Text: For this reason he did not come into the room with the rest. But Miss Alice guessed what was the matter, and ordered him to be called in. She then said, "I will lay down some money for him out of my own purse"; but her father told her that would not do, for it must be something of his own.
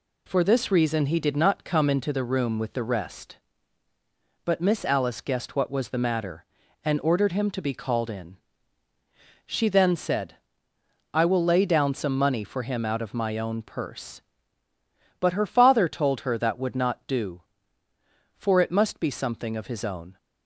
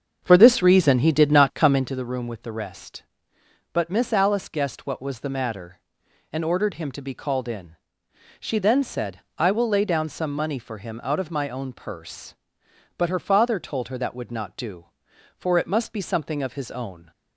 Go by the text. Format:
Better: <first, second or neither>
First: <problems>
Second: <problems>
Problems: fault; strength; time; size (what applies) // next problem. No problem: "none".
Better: first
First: none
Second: starts louder than the rest; strong; until 2.0 s; 7 dB